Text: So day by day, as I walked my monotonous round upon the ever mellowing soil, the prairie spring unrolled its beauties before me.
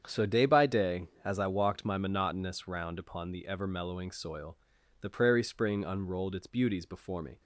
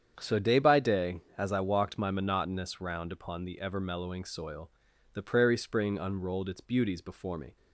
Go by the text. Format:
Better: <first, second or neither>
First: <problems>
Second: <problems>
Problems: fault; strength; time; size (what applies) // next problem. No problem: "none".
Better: neither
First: starts louder than the rest; strong; until 1.0 s; 8 dB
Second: starts louder than the rest; strong; until 1.2 s; 8 dB